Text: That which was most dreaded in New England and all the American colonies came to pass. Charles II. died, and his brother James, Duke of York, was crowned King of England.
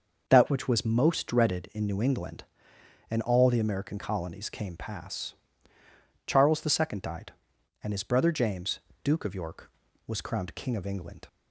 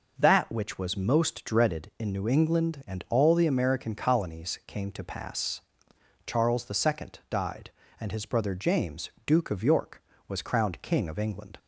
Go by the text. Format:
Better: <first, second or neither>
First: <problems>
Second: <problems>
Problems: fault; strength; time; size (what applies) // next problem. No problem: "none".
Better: second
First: starts louder than the rest; noticeable; until 1.2 s; 6 dB // skips "to"; at 4.7 s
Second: none